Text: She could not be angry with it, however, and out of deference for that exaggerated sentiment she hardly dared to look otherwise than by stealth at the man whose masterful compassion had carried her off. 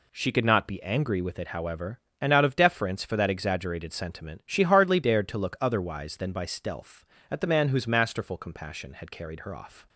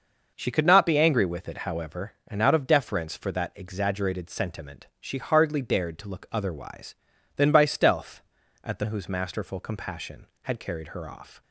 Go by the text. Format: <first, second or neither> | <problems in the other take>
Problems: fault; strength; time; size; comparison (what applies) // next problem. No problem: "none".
first | skips "man"; at 8.8 s